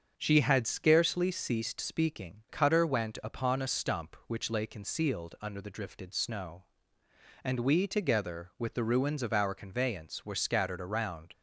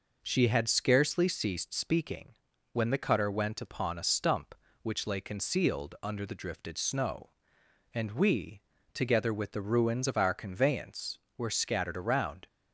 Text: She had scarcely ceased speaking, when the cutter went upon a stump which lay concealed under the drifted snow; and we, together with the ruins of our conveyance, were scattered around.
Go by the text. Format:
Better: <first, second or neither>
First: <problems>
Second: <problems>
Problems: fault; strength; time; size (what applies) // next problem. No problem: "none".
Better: second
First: starts louder than the rest; strong; until 1.1 s; 7 dB // skips "when the"; at 2.4 s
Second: none